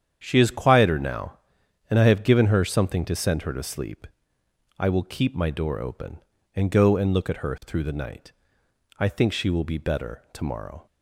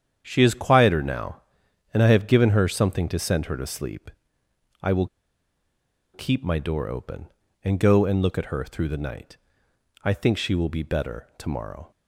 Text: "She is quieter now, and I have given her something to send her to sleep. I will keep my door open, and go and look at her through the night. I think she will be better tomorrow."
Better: first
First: starts louder than the rest; strong; until 1.2 s; 8.5 dB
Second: starts louder than the rest; strong; until 1.2 s; 8.5 dB // pauses between "will" and "keep"; at 5.0 s; 1.0 s long

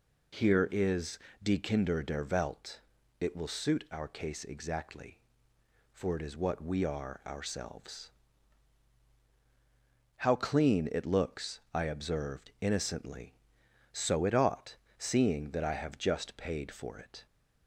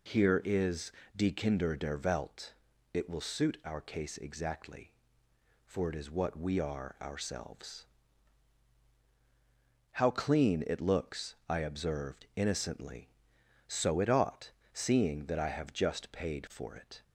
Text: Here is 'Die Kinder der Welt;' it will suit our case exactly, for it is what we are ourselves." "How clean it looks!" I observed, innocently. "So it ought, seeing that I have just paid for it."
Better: neither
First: pauses between "is" and "Die"; slight; at 1.1 s; 0.24 s long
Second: pauses between "is" and "Die"; slight; at 0.9 s; 0.24 s long

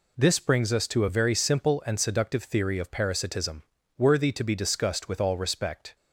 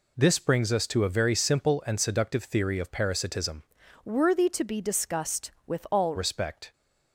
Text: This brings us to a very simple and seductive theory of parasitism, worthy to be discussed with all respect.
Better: first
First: none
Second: changes voice from "worthy" to "all"; from 4.0 to 6.1 s; 2.1 s long

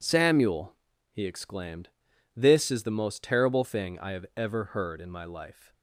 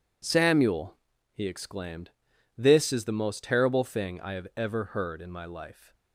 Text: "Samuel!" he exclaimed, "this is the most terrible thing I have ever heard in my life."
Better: neither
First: none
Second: none

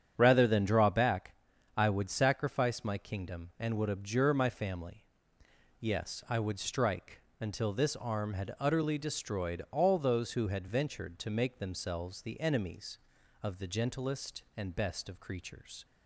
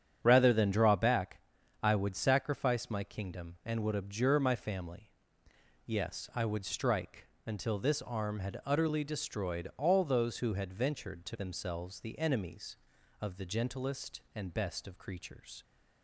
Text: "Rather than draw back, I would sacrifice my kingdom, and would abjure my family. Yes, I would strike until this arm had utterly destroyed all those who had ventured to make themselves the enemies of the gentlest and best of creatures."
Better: first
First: starts louder than the rest; strong; until 1.1 s; 8.5 dB // pauses between "strike" and "until"; slight; at 7.2 s; 0.20 s long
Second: starts louder than the rest; strong; until 1.2 s; 9 dB // pauses between "strike" and "until"; slight; at 7.2 s; 0.20 s long // skips "make"; at 11.3 s

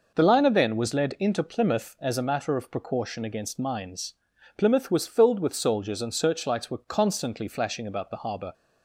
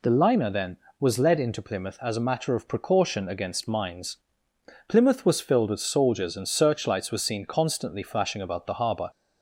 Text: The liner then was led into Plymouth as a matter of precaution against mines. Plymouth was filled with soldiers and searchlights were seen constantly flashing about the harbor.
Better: second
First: skips "seen"; at 6.8 s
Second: none

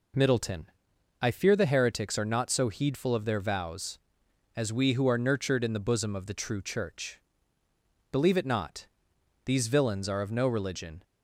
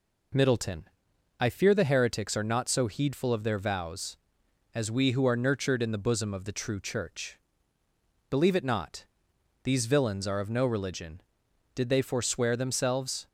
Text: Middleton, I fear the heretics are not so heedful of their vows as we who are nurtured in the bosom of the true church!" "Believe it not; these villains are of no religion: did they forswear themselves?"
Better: second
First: stops before "did they forswear themselves"; at 11.0 s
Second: none

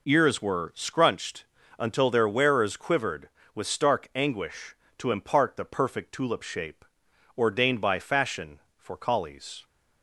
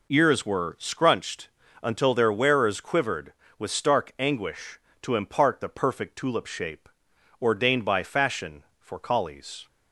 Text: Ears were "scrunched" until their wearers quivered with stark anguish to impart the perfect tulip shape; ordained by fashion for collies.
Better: neither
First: pauses between "scrunched" and "until"; slight; at 1.4 s; 0.34 s long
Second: pauses between "scrunched" and "until"; slight; at 1.4 s; 0.34 s long

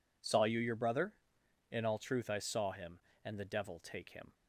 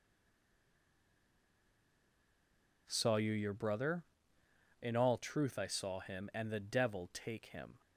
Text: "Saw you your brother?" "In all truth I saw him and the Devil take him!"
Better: first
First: none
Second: stays silent before the first word; strong; until 2.8 s; 2.8 s long

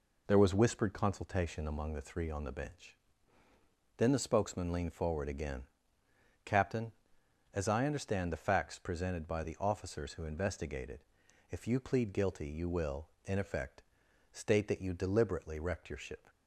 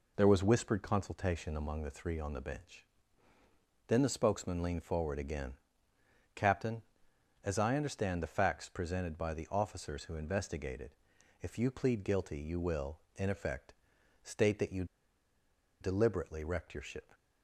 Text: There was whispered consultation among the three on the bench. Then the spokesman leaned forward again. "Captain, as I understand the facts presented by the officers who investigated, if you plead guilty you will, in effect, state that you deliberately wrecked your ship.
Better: first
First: none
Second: pauses between "you" and "deliberately"; noticeable; at 14.8 s; 0.96 s long

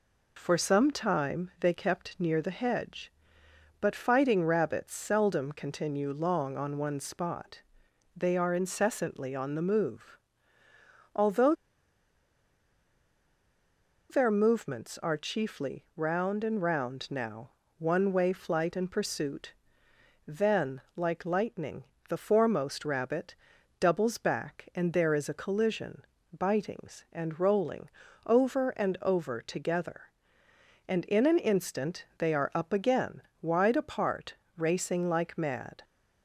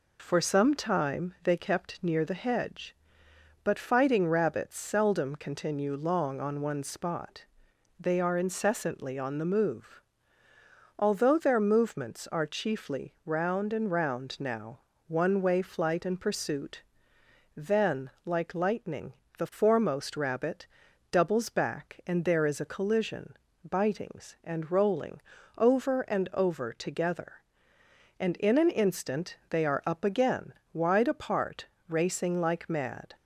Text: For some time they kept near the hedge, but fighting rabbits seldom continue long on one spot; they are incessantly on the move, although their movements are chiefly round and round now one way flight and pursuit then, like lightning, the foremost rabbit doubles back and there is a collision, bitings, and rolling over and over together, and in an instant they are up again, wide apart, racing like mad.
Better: second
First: pauses between "although" and "their"; strong; at 11.5 s; 2.5 s long // pauses between "now" and "one"; slight; at 17.4 s; 0.30 s long // pauses between "pursuit" and "then"; noticeable; at 19.5 s; 0.74 s long // pauses between "rabbit" and "doubles"; noticeable; at 23.3 s; 0.46 s long // pauses between "rolling" and "over"; at 27.8 s; 0.38 s long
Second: pauses between "now" and "one"; slight; at 14.7 s; 0.30 s long // pauses between "pursuit" and "then"; noticeable; at 16.8 s; 0.74 s long // pauses between "rabbit" and "doubles"; noticeable; at 20.6 s; 0.46 s long // pauses between "rolling" and "over"; at 25.2 s; 0.38 s long

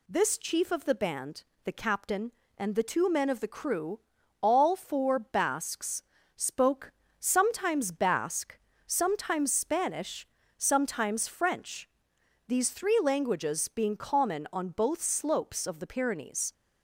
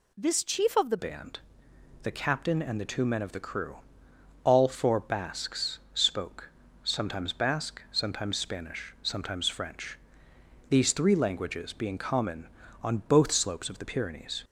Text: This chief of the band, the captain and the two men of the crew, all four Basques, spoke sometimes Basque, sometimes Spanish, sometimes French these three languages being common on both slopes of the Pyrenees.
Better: first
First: pauses between "spoke" and "sometimes"; slight; at 6.9 s; 0.26 s long // pauses between "French" and "these"; noticeable; at 11.8 s; 0.58 s long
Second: changes voice at "band"; from 0.9 s on; 13.5 s long // pauses between "spoke" and "sometimes"; slight; at 6.4 s; 0.34 s long // pauses between "French" and "these"; noticeable; at 9.9 s; 0.70 s long

